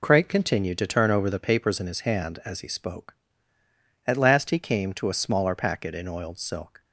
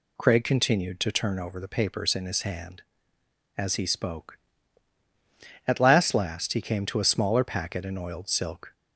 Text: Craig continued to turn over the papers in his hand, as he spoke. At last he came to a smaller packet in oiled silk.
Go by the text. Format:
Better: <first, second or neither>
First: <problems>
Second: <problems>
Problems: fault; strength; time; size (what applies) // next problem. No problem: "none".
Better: first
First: none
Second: says "last" twice; at 6.1 s